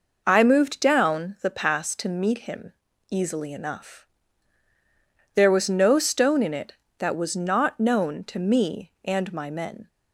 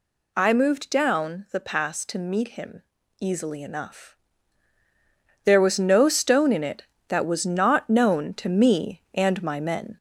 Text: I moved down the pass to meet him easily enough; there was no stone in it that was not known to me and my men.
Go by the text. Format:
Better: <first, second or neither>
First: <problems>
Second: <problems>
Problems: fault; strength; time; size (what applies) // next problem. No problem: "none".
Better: first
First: pauses between "him" and "easily"; slight; at 2.7 s; 0.36 s long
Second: gets louder; slight; throughout; 2.5 dB // pauses between "him" and "easily"; slight; at 2.8 s; 0.36 s long